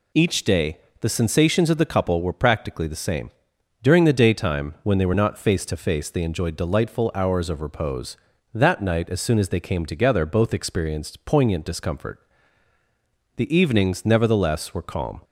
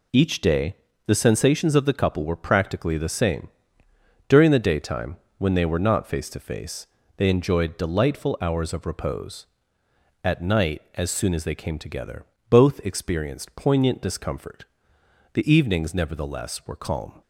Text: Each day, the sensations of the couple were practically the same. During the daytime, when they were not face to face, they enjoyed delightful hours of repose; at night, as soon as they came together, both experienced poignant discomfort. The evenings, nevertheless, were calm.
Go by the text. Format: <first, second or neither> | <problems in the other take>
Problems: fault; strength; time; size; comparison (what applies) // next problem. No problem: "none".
second | says "that" for "at"; at 8.5 s